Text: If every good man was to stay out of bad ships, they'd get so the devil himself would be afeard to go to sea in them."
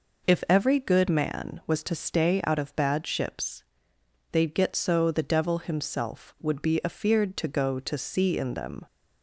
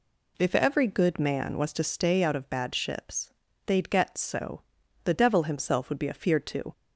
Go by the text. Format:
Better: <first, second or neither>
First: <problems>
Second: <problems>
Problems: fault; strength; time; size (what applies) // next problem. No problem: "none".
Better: first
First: none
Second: pauses between "so" and "the"; at 4.6 s; 0.42 s long // stops before "go to sea in them"; at 6.7 s